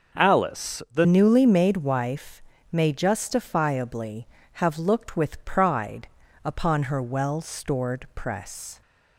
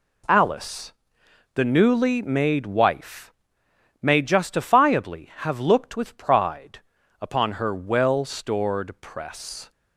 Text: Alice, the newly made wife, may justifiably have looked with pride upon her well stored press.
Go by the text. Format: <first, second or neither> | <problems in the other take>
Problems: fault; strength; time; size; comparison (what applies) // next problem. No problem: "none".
second | changes voice at "newly"; from 1.0 s on; 7.8 s long // pauses between "pride" and "upon"; slight; at 6.0 s; 0.36 s long; also in the second